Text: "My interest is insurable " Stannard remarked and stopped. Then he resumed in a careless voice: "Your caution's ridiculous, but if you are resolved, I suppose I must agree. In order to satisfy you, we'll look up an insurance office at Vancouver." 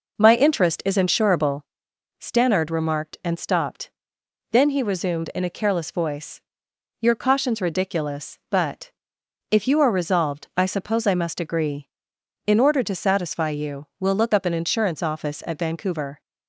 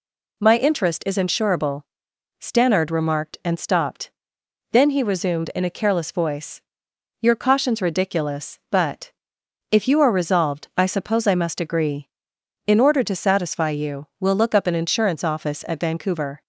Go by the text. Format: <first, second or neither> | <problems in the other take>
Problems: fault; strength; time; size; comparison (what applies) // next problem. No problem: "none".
second | starts louder than the rest; noticeable; until 1.6 s; 5 dB // pauses between "but" and "if"; noticeable; at 8.9 s; 0.58 s long; noticeable in the second